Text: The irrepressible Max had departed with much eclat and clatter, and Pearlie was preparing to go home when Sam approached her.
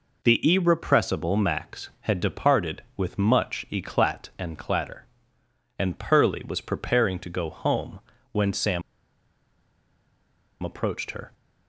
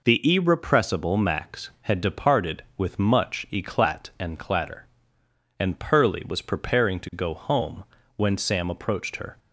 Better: second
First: pauses between "home" and "when"; slight; at 8.0 s; 0.32 s long // pauses between "Sam" and "approached"; strong; at 8.8 s; 1.8 s long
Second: pauses between "home" and "when"; slight; at 7.8 s; 0.32 s long

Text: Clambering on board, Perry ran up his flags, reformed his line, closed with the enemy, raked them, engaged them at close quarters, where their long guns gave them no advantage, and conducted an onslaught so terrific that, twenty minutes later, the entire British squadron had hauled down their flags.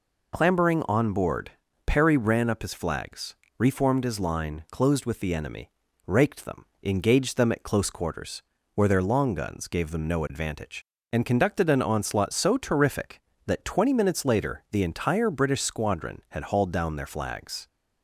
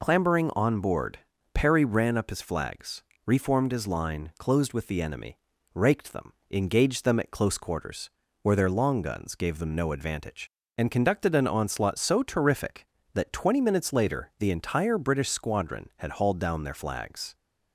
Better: neither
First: none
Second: none

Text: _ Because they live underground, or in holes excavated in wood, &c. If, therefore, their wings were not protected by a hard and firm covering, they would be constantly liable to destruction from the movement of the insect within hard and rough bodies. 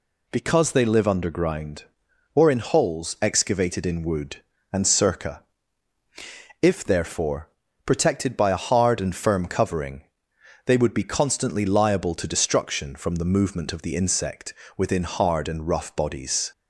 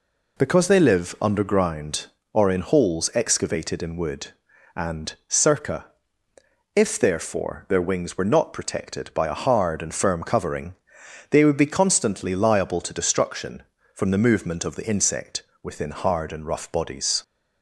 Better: second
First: skips "their wings were not"; at 7.6 s // pauses between "insect" and "within"; slight; at 14.5 s; 0.24 s long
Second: pauses between "insect" and "within"; slight; at 15.4 s; 0.22 s long

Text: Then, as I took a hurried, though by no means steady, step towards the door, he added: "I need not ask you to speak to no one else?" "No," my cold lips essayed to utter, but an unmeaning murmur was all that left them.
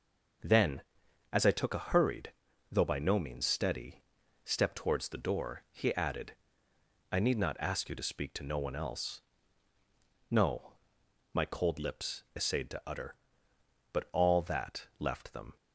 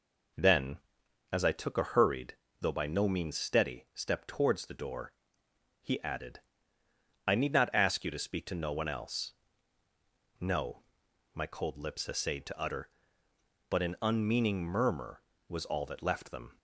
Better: second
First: skips "an unmeaning murmur was"; at 14.1 s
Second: none

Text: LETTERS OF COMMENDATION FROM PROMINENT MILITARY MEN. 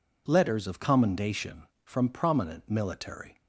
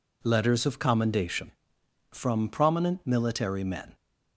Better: second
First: stops before "MEN"; at 3.4 s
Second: none

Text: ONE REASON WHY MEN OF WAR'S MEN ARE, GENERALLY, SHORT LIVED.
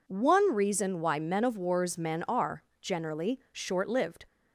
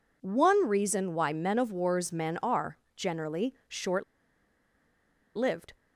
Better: first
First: none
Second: pauses between "SHORT" and "LIVED"; strong; at 4.0 s; 1.3 s long

